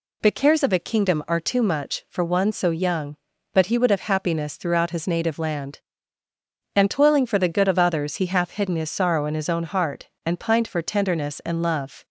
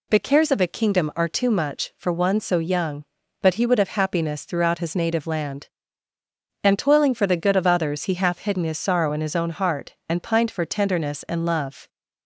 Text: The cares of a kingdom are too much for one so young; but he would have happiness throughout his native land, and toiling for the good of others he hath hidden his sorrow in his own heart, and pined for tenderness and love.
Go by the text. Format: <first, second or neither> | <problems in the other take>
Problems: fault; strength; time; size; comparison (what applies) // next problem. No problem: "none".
neither | none